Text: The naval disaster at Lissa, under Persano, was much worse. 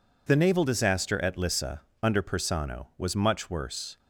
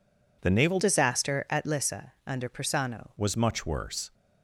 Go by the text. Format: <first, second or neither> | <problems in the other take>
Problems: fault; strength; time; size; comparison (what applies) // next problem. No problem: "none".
first | changes voice from "disaster" to "Persano"; from 0.8 to 3.0 s; 2.2 s long